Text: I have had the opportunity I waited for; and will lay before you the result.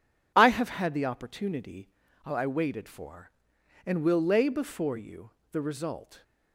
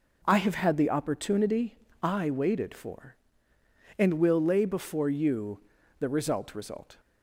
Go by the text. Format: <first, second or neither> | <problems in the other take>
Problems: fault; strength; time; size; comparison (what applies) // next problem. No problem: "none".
first | pauses between "opportunity" and "I"; slight; at 1.7 s; 0.26 s long; slight in the first // pauses between "you" and "the"; at 5.5 s; 0.40 s long; slight in the first // says "result" twice; at 6.5 s